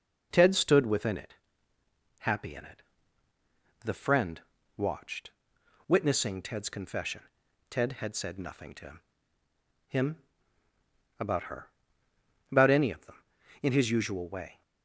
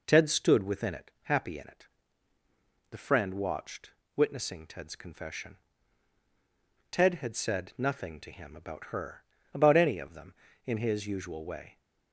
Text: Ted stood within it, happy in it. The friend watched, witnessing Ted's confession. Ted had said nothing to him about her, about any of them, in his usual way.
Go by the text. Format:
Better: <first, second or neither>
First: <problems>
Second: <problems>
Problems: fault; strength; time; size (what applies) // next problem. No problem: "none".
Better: second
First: pauses between "friend" and "watched"; at 4.3 s; 0.38 s long // says "him" twice; at 9.8 s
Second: none